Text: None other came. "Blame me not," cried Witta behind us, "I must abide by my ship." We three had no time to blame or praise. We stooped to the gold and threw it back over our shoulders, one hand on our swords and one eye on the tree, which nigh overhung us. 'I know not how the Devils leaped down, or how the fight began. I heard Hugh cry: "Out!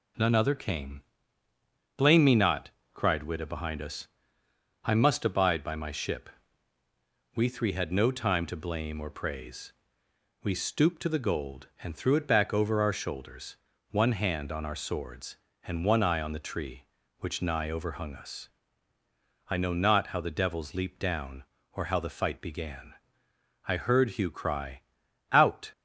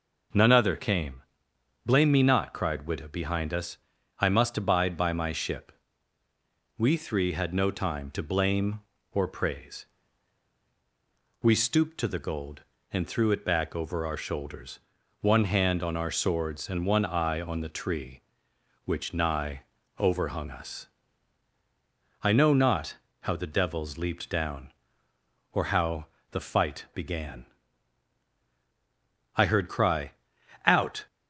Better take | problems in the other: first | pauses between "nigh" and "overhung"; slight; at 19.6 s; 0.36 s long // pauses between "not" and "how"; slight; at 22.9 s; 0.24 s long // pauses between "how" and "the"; slight; at 26.0 s; 0.24 s long // skips "Hugh"; at 29.6 s

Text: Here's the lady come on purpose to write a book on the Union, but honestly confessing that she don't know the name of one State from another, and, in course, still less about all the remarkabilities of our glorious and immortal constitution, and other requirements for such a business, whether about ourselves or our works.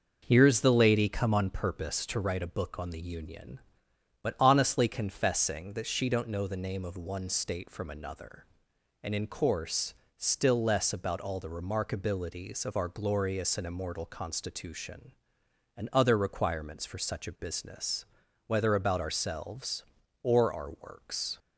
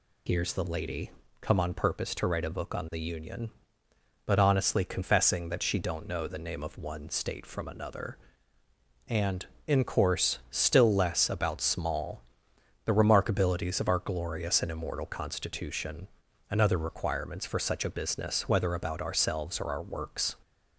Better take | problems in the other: first | pauses between "lady" and "come"; slight; at 1.0 s; 0.30 s long // says "small" for "all"; at 11.5 s

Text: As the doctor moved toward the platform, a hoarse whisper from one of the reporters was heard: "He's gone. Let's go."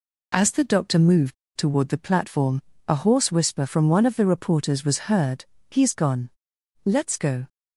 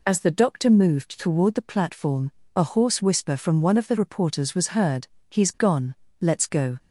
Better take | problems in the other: second | pauses between "moved" and "toward"; slight; at 1.3 s; 0.23 s long

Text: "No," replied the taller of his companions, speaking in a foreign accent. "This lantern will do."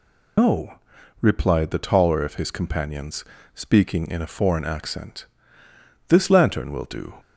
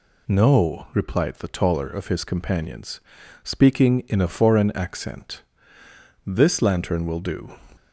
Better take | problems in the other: second | loses the start of "No"; at 0.3 s; 155 ms

